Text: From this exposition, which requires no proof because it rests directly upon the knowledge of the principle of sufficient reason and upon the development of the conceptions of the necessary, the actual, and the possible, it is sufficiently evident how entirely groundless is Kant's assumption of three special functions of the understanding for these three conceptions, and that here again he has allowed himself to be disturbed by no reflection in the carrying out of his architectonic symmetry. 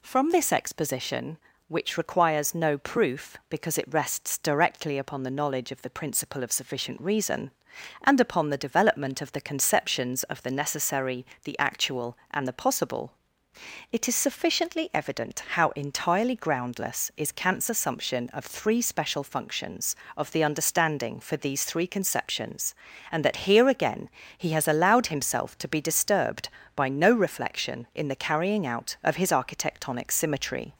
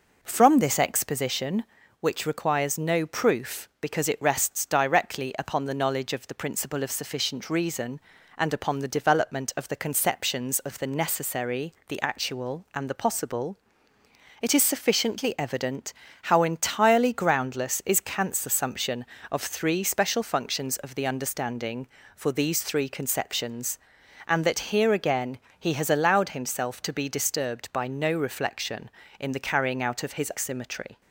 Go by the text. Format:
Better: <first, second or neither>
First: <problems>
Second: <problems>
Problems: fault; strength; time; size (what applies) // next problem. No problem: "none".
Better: first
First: pauses between "again" and "he"; slight; at 24.0 s; 0.28 s long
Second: pauses between "evident" and "how"; slight; at 15.9 s; 0.30 s long // pauses between "again" and "he"; slight; at 25.3 s; 0.22 s long // skips "architectonic"; at 30.3 s